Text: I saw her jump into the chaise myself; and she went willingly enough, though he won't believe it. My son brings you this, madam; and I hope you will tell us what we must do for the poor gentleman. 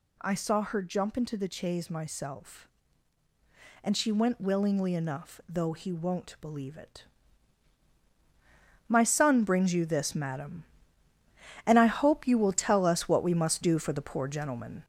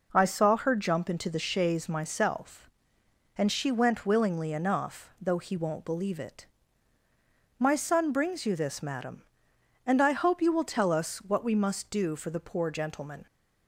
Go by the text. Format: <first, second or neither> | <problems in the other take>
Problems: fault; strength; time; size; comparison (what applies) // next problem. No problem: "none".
second | gets louder; noticeable; throughout; 4.5 dB